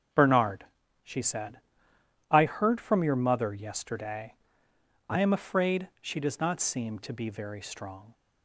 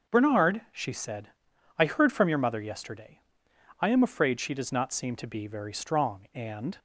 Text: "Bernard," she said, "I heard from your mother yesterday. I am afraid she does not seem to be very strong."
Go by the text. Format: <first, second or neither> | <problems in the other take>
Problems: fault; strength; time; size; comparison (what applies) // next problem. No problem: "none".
first | starts louder than the rest; until 1.2 s; 7 dB; strong in the first // goes on to say "And"; slight; from 6.3 s on; 0.44 s long